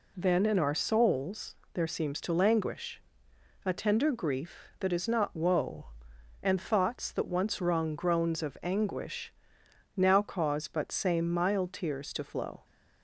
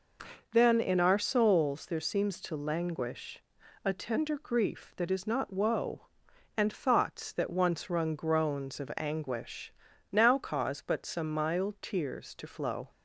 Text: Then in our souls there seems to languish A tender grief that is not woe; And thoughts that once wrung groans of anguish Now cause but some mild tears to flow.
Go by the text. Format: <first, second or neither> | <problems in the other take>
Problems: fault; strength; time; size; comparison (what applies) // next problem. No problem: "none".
second | pauses between "souls" and "there"; slight; at 1.5 s; 0.20 s long // pauses between "languish" and "A"; noticeable; at 3.0 s; 0.64 s long; also in the second // pauses between "anguish" and "Now"; noticeable; at 9.3 s; 0.64 s long; also in the second // says "same" for "some"; at 10.9 s